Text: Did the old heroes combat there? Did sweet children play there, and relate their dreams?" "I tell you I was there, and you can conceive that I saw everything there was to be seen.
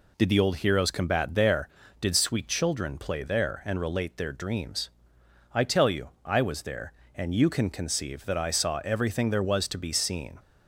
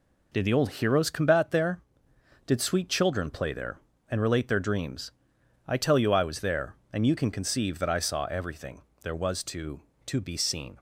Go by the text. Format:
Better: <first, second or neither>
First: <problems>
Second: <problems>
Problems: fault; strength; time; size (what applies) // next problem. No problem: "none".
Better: first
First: none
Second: pauses between "everything" and "there"; slight; at 8.8 s; 0.20 s long // says "to" twice; at 10.0 s